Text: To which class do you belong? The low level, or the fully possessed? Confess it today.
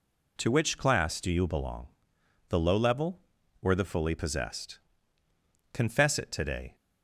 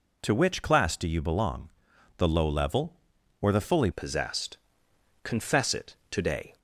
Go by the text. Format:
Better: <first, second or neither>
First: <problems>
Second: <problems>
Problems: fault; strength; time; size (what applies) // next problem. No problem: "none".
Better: first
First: none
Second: changes voice at "possessed"; from 3.9 s on; 2.6 s long // pauses between "it" and "today"; slight; at 5.9 s; 0.16 s long